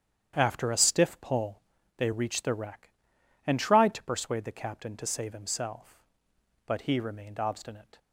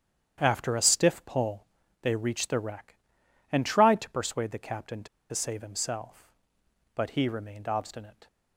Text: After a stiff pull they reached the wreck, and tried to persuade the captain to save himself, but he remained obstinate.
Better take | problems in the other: first | starts louder than the rest; strong; until 1.4 s; 9.5 dB; strong in the first // pauses between "pull" and "they"; slight; at 1.6 s; 0.36 s long; slight in the first // pauses between "to" and "save"; slight; at 5.0 s; 0.25 s long

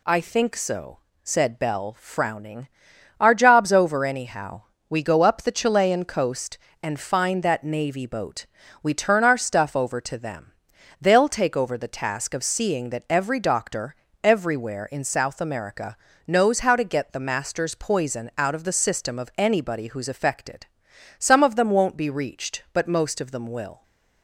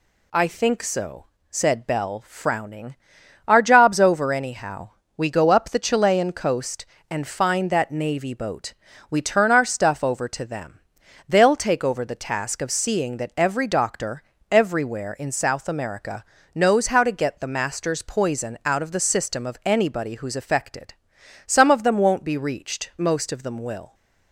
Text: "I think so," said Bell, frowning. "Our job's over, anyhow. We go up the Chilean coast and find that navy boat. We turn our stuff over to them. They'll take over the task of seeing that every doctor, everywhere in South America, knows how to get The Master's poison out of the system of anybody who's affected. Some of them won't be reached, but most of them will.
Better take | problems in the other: first | skips "but"; at 22.9 s

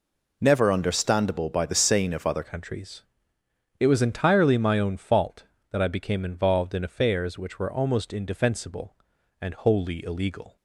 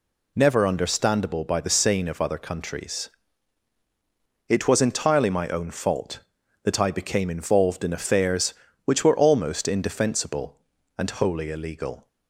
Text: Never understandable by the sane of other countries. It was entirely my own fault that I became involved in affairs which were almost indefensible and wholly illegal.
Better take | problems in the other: second | changes voice at "countries"; from 2.4 s on; 8.1 s long

